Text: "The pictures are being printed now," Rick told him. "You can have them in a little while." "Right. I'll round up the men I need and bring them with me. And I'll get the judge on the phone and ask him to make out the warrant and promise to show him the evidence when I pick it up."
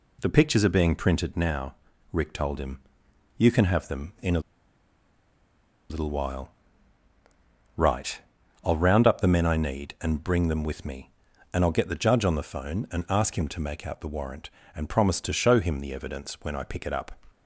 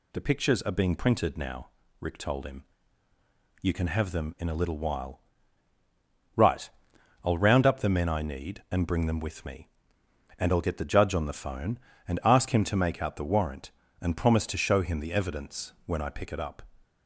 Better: second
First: pauses between "a" and "little"; strong; at 4.3 s; 1.5 s long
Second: none

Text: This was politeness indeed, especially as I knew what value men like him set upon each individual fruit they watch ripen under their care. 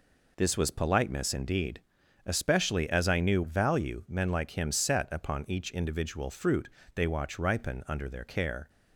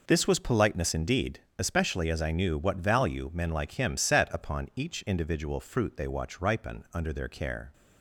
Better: second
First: skips "what"; at 3.4 s // pauses between "fruit" and "they"; slight; at 6.6 s; 0.26 s long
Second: none

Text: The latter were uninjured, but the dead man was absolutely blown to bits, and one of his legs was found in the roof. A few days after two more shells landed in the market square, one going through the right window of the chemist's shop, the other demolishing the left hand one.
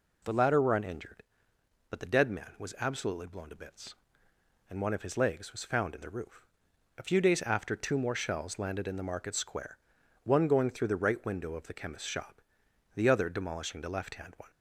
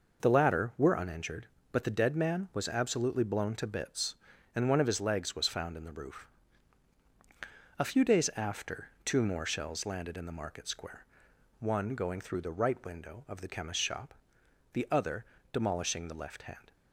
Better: first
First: none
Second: pauses between "other" and "demolishing"; slight; at 15.2 s; 0.34 s long // stops before "one"; at 16.7 s

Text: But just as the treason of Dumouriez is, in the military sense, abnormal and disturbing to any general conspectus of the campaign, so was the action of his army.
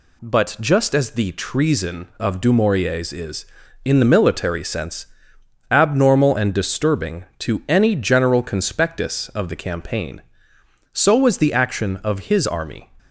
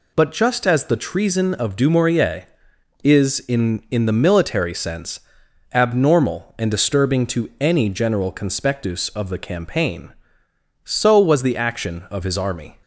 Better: first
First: none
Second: says "in" twice; at 3.8 s

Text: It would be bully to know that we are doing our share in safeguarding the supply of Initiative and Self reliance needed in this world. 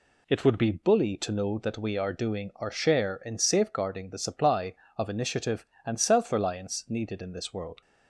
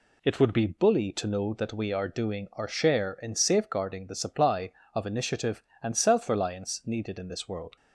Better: neither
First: none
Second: none

